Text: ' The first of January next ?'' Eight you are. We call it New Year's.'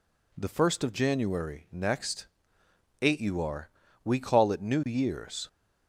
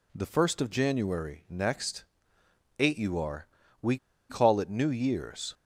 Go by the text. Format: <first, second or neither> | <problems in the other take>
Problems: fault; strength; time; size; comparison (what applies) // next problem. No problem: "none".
first | pauses between "We" and "call"; slight; at 3.9 s; 0.32 s long